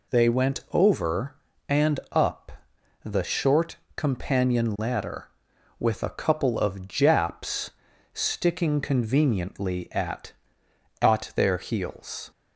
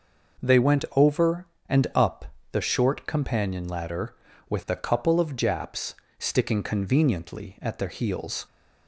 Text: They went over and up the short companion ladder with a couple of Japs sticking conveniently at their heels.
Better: second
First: pauses between "up" and "the"; noticeable; at 2.5 s; 0.52 s long // pauses between "short" and "companion"; slight; at 3.7 s; 0.20 s long // pauses between "Japs" and "sticking"; at 7.7 s; 0.42 s long // says "at" twice; at 11.0 s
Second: pauses between "up" and "the"; slight; at 2.2 s; 0.26 s long // pauses between "Japs" and "sticking"; slight; at 5.9 s; 0.24 s long

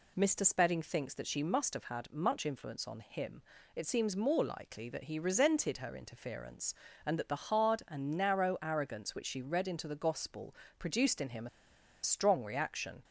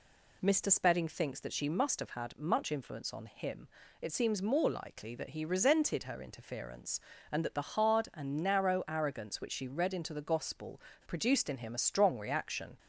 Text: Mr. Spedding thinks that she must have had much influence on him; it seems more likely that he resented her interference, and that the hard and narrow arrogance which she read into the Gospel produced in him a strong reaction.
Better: second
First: pauses between "Gospel" and "produced"; slight; at 10.5 s; 0.24 s long // pauses between "him" and "a"; noticeable; at 11.4 s; 0.55 s long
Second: pauses between "Gospel" and "produced"; slight; at 10.7 s; 0.26 s long

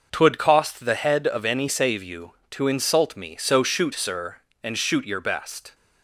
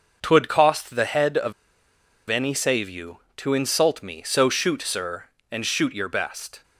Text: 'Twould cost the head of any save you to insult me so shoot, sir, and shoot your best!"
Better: first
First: none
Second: pauses between "of" and "any"; noticeable; at 1.5 s; 0.77 s long

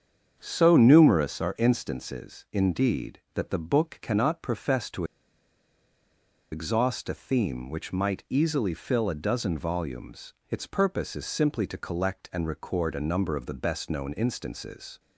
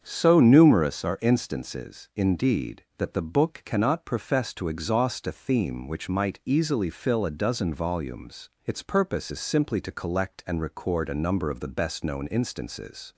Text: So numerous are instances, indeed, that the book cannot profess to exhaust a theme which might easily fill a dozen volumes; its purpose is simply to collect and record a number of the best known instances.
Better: second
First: starts louder than the rest; strong; until 1.4 s; 7.5 dB // pauses between "to" and "exhaust"; strong; at 5.0 s; 1.4 s long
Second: starts louder than the rest; strong; until 1.0 s; 7.5 dB

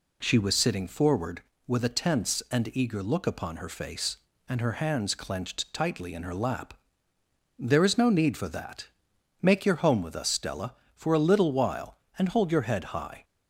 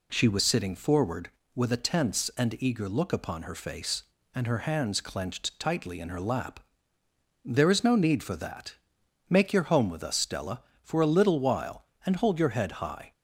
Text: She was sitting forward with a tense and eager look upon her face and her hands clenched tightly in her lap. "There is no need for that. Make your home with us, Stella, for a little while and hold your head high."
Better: neither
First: none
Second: none

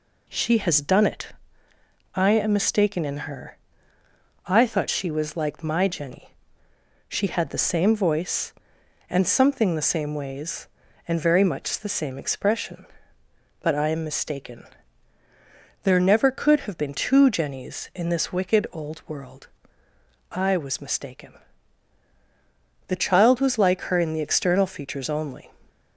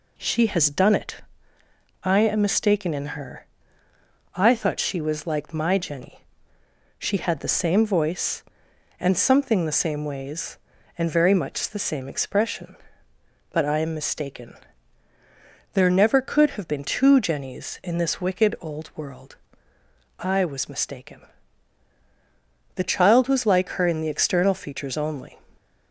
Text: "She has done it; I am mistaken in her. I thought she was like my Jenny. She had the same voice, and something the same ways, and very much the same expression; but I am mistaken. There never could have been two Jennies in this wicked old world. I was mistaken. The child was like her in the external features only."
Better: neither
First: none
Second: none

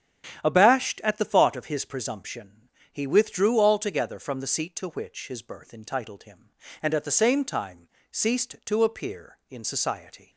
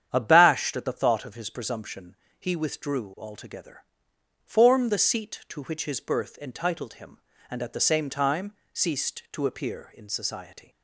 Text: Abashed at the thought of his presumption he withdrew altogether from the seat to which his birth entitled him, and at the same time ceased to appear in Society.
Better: first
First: starts louder than the rest; strong; until 1.4 s; 9.5 dB // pauses between "presumption" and "he"; slight; at 2.6 s; 0.22 s long // pauses between "time" and "ceased"; slight; at 7.8 s; 0.20 s long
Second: starts louder than the rest; strong; until 1.1 s; 9 dB // pauses between "presumption" and "he"; slight; at 2.1 s; 0.24 s long // says "form" for "from"; at 4.4 s // pauses between "time" and "ceased"; slight; at 8.5 s; 0.22 s long

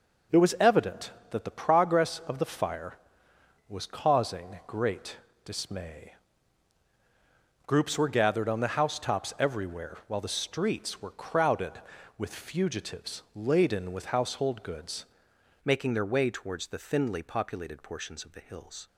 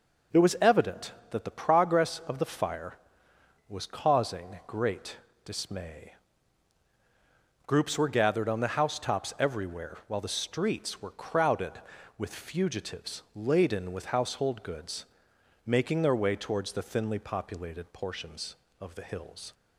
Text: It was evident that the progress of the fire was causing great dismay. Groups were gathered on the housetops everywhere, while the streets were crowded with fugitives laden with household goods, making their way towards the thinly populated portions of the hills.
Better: second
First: pauses between "great" and "dismay"; slight; at 5.1 s; 0.26 s long // changes voice at "making"; from 15.6 s on; 3.2 s long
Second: pauses between "great" and "dismay"; slight; at 5.1 s; 0.26 s long

